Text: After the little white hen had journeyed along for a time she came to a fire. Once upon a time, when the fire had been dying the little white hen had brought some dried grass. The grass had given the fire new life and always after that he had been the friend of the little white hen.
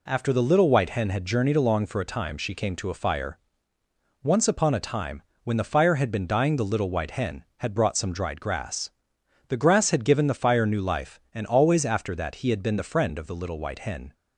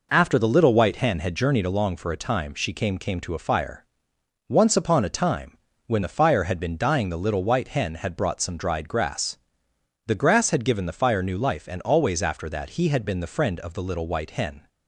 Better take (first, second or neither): first